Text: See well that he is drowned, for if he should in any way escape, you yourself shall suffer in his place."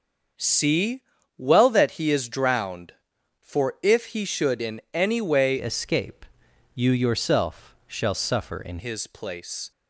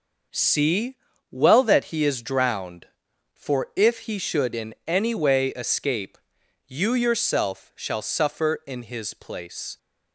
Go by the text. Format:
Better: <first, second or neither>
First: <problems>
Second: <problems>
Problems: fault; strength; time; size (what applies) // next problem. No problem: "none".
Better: second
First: starts louder than the rest; until 1.7 s; 6 dB // pauses between "See" and "well"; slight; at 1.0 s; 0.36 s long // changes voice from "escape" to "in"; from 5.5 to 8.7 s; 3.2 s long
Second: pauses between "See" and "well"; slight; at 0.9 s; 0.35 s long